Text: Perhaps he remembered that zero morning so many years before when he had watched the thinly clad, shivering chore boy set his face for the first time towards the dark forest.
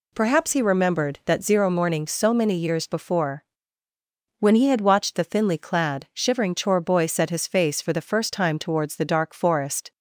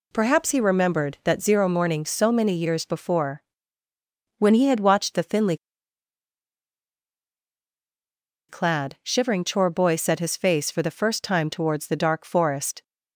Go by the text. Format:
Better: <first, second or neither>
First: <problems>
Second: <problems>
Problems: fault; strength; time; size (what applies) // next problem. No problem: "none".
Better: first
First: pauses between "before" and "when"; noticeable; at 3.4 s; 0.95 s long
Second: pauses between "before" and "when"; noticeable; at 3.4 s; 0.96 s long // pauses between "thinly" and "clad"; strong; at 5.5 s; 2.9 s long